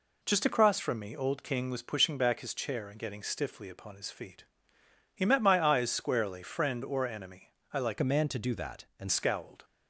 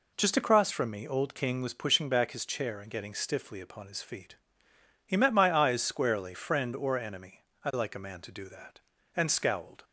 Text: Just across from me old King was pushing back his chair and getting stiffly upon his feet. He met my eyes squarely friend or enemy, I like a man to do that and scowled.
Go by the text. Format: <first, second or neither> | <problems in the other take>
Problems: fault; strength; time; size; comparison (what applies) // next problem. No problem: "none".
second | changes voice from "a" to "and"; from 8.0 to 9.0 s; 1.0 s long